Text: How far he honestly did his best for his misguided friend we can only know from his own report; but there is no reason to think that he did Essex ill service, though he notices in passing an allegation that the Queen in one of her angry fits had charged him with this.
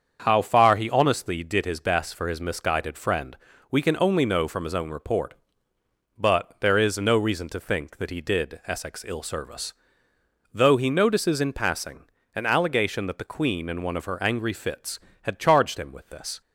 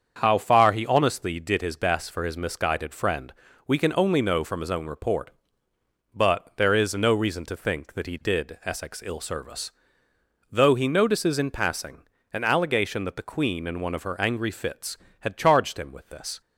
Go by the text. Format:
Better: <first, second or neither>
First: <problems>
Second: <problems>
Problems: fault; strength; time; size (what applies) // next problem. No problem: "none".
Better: neither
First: starts louder than the rest; strong; until 1.2 s; 7 dB // pauses between "friend" and "we"; slight; at 3.3 s; 0.36 s long // pauses between "passing" and "an"; slight; at 12.0 s; 0.30 s long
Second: starts louder than the rest; strong; until 1.2 s; 7 dB // pauses between "friend" and "we"; slight; at 3.3 s; 0.36 s long // pauses between "passing" and "an"; slight; at 12.0 s; 0.30 s long